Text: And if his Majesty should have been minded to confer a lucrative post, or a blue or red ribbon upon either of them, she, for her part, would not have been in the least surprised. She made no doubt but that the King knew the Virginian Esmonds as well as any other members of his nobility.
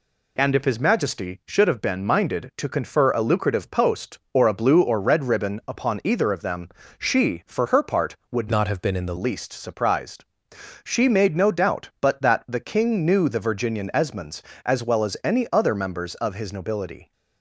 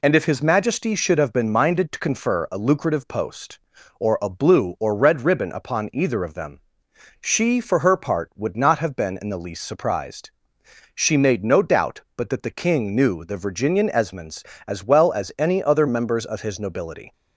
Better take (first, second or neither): second